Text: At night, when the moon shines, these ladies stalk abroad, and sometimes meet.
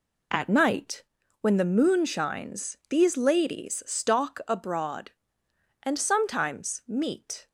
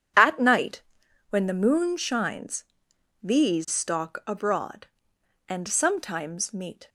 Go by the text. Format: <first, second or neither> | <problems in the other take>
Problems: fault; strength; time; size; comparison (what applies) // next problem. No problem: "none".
first | skips "ladies"; at 3.6 s